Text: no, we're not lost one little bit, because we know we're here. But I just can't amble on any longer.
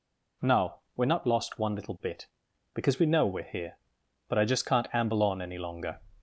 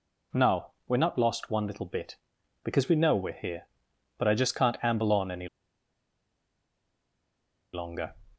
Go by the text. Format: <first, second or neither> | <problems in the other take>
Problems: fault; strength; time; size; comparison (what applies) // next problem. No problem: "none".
first | pauses between "any" and "longer"; strong; at 5.4 s; 2.2 s long